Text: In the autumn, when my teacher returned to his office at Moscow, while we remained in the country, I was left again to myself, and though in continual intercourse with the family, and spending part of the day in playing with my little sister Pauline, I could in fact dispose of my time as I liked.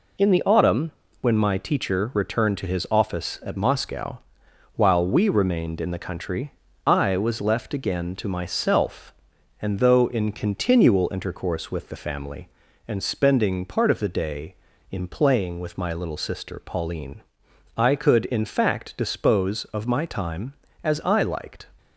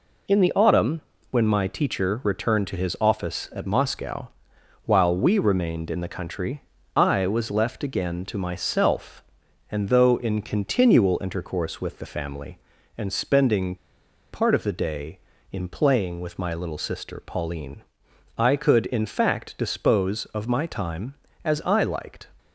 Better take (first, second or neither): first